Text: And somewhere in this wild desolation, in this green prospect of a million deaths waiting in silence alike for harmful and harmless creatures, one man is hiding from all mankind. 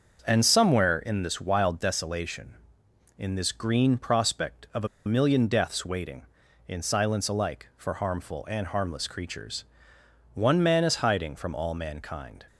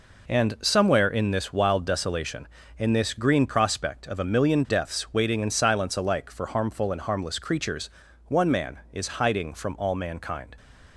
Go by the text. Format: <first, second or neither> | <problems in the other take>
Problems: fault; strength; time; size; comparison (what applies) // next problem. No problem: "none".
second | starts louder than the rest; until 1.2 s; 6.5 dB // pauses between "a" and "million"; slight; at 4.8 s; 0.18 s long